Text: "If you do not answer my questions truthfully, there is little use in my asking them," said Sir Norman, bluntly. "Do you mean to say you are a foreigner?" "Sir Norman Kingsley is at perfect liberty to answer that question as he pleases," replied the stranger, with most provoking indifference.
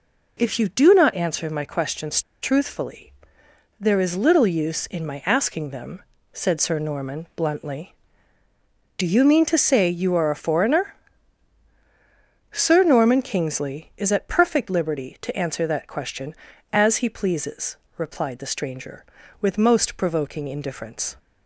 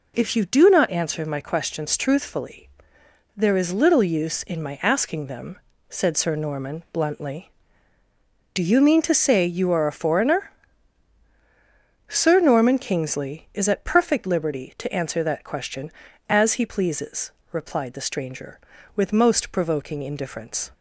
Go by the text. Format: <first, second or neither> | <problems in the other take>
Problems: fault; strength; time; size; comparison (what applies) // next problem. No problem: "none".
second | pauses between "questions" and "truthfully"; slight; at 2.2 s; 0.22 s long